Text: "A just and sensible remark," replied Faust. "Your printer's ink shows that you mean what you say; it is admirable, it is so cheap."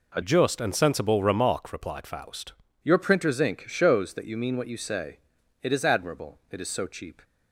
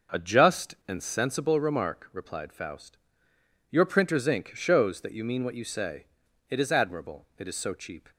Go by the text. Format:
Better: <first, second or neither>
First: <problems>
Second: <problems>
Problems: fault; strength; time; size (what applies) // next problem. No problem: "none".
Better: second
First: changes voice from "just" to "Faust"; from 0.2 to 2.5 s; 2.3 s long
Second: none